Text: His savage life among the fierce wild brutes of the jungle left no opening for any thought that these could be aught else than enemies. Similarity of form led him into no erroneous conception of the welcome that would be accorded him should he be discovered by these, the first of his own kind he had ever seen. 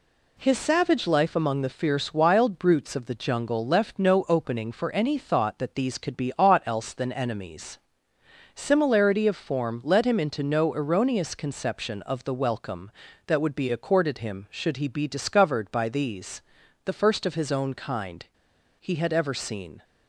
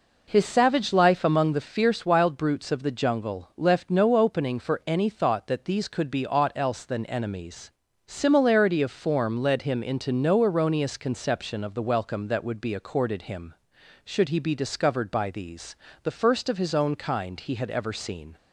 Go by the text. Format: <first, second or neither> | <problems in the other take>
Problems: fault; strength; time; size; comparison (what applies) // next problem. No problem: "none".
second | pauses between "kind" and "he"; noticeable; at 18.2 s; 0.53 s long